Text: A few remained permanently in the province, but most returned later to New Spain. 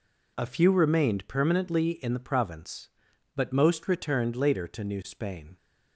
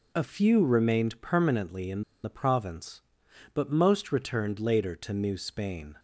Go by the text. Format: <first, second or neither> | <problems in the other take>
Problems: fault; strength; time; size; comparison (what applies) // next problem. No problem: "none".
first | pauses between "in" and "the"; slight; at 2.0 s; 0.22 s long